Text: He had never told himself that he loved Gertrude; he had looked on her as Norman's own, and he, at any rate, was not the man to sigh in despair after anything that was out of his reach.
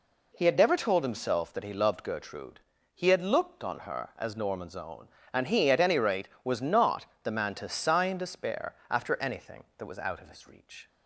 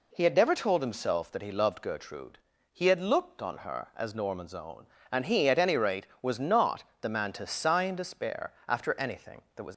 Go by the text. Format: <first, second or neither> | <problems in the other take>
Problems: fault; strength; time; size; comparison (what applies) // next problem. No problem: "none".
first | pauses between "not" and "the"; slight; at 6.8 s; 0.18 s long; slight in the first // pauses between "despair" and "after"; slight; at 8.5 s; 0.16 s long; slight in the first // stops before "out of his reach"; at 9.7 s